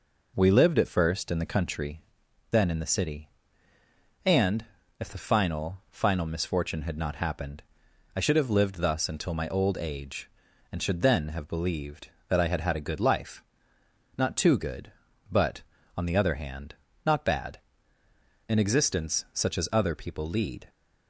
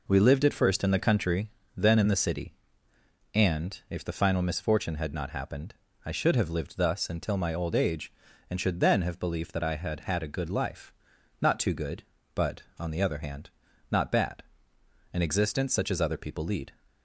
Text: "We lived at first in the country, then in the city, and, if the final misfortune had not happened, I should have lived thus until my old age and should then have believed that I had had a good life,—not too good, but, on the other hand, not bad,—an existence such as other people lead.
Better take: second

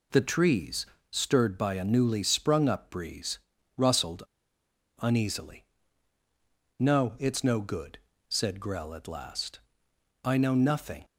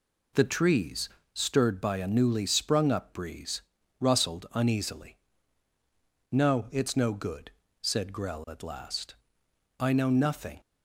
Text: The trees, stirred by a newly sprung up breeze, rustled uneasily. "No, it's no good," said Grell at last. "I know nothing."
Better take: second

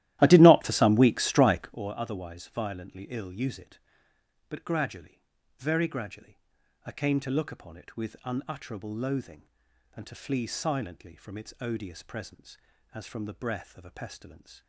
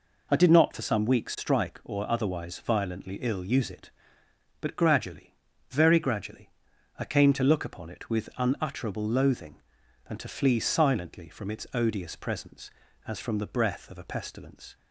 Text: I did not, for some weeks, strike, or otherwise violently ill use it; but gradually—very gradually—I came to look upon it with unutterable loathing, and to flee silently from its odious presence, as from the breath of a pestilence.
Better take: second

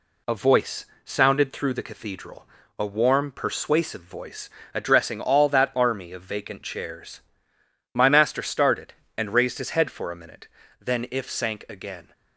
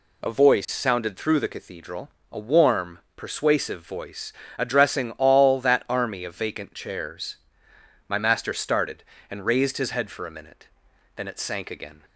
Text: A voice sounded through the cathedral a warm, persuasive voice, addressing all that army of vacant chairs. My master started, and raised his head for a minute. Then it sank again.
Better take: second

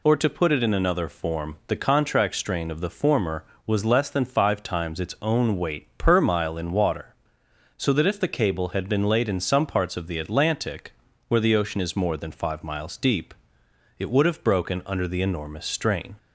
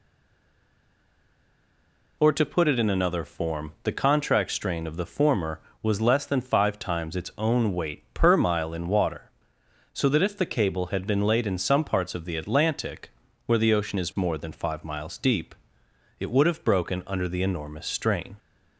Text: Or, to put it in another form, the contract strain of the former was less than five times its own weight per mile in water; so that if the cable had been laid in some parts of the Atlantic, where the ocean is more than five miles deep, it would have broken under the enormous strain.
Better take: first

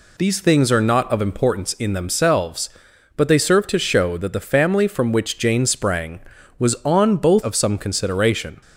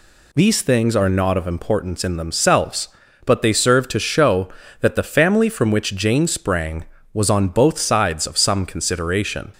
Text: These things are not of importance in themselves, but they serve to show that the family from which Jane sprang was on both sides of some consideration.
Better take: second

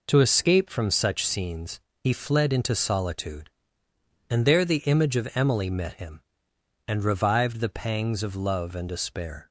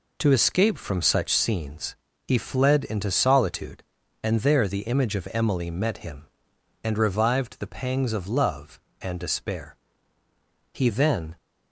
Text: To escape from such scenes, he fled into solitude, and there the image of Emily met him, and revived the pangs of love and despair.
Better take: first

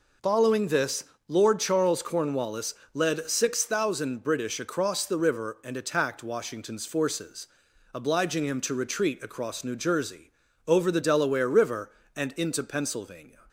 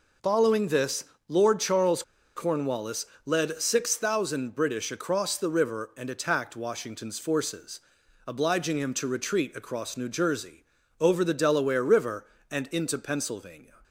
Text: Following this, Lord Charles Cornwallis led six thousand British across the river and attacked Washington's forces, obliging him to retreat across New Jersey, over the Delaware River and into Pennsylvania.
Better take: first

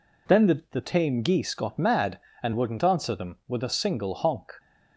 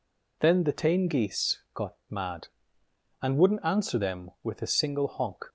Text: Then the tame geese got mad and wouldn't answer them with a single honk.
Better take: second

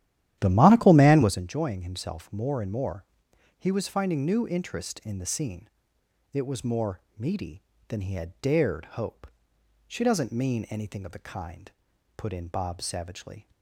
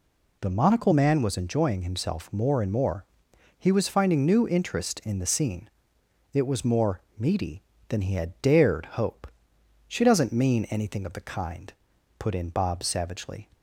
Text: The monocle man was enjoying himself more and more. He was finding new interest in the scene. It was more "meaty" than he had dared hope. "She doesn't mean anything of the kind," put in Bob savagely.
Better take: second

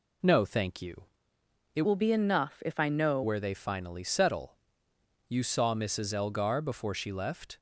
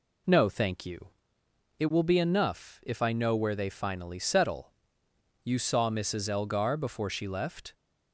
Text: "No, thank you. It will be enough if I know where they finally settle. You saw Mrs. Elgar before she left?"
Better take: second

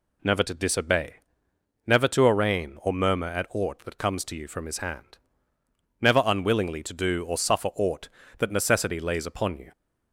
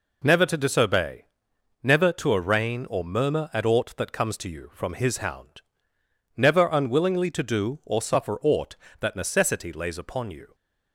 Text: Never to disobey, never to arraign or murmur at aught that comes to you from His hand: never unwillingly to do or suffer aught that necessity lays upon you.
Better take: first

